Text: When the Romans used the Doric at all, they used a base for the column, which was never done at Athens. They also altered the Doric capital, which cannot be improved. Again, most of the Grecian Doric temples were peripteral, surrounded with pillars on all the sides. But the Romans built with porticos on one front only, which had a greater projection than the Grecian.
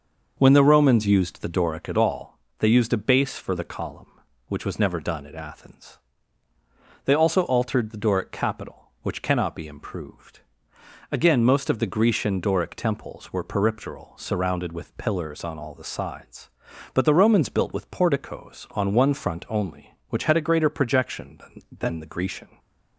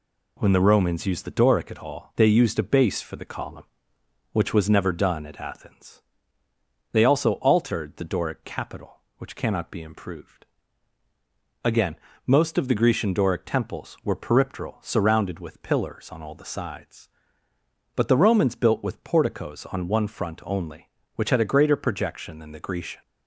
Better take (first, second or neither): second